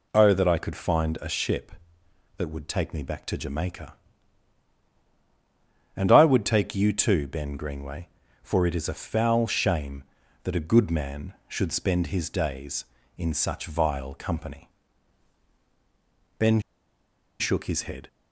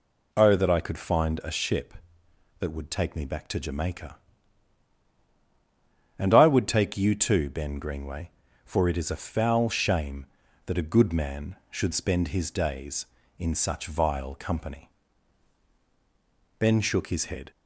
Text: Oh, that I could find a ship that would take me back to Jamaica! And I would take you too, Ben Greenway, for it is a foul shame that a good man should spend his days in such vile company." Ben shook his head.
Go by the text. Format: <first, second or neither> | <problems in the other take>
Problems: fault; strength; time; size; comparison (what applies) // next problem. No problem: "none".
second | pauses between "Ben" and "shook"; noticeable; at 16.5 s; 0.80 s long